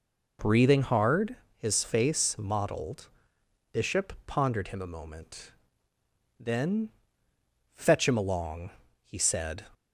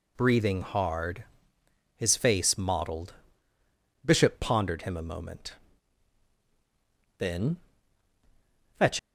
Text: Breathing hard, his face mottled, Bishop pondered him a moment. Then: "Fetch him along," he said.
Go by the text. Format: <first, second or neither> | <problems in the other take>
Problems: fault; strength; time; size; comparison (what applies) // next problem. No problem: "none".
first | stops before "him along he said"; at 8.9 s